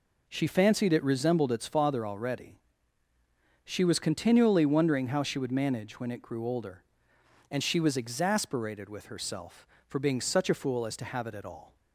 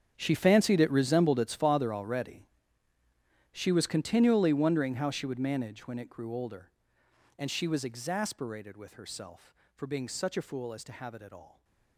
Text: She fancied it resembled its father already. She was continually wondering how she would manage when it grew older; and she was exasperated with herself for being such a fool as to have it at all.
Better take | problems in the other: first | gets quieter; strong; throughout; 17.5 dB

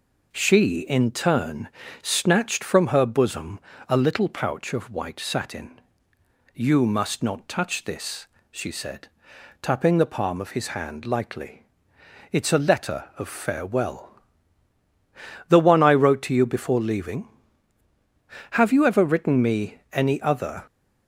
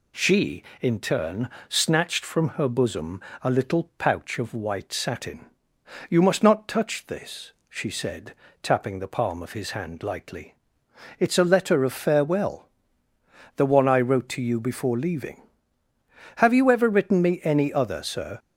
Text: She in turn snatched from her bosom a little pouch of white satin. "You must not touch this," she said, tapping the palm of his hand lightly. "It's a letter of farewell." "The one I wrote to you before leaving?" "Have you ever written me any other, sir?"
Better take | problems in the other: second | pauses between "turn" and "snatched"; slight; at 1.6 s; 0.34 s long; slight in the second // pauses between "bosom" and "a"; slight; at 3.5 s; 0.28 s long; slight in the second // stops before "sir"; at 20.6 s

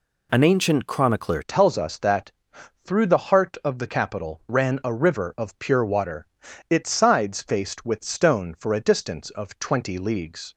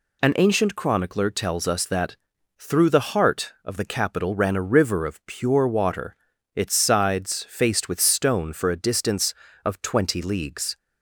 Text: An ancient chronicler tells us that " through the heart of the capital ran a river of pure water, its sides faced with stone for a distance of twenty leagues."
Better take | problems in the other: second | changes voice at "tells"; from 1.4 s on; 9.1 s long

